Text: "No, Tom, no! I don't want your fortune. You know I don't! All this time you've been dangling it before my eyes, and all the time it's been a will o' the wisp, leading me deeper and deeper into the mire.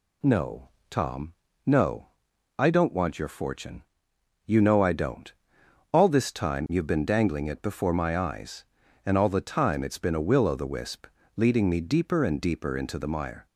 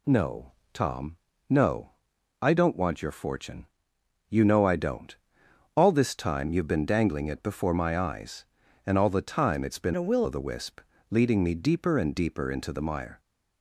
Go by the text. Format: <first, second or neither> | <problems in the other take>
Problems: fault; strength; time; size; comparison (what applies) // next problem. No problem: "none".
first | changes voice from "a" to "will"; from 9.9 to 10.2 s; 0.3 s long